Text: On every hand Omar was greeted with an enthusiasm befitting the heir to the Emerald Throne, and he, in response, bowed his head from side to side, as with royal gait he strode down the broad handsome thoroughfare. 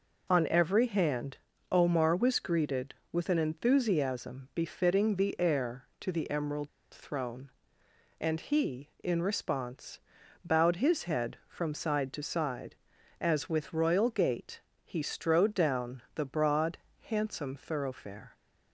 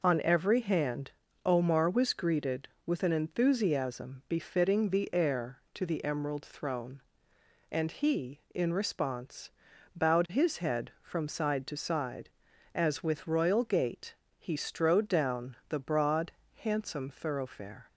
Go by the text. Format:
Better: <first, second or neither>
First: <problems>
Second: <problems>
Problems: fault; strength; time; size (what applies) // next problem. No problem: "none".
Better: second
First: pauses between "hand" and "Omar"; slight; at 1.3 s; 0.32 s long // pauses between "Emerald" and "Throne"; slight; at 6.6 s; 0.24 s long // pauses between "gait" and "he"; slight; at 14.5 s; 0.24 s long // pauses between "broad" and "handsome"; slight; at 16.7 s; 0.22 s long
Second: pauses between "hand" and "Omar"; slight; at 1.1 s; 0.32 s long // pauses between "gait" and "he"; slight; at 14.1 s; 0.24 s long // pauses between "broad" and "handsome"; slight; at 16.3 s; 0.22 s long